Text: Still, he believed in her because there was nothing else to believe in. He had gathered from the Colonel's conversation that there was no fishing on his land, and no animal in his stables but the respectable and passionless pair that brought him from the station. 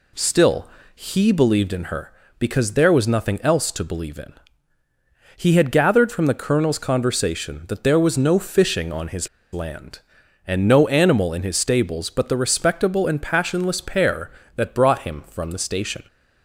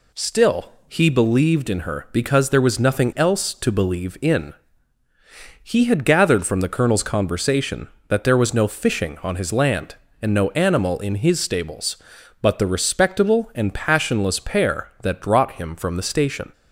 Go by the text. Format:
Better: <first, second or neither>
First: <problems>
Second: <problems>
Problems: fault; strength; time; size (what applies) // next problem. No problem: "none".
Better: second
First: pauses between "his" and "land"; slight; at 9.2 s; 0.24 s long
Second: none